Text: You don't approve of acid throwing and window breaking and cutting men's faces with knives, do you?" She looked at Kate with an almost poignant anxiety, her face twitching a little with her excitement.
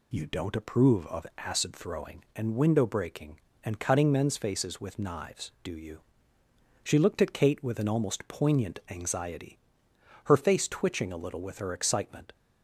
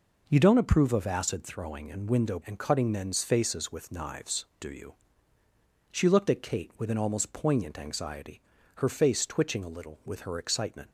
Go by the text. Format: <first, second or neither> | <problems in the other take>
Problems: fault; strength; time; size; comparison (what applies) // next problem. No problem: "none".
first | skips "breaking"; at 2.4 s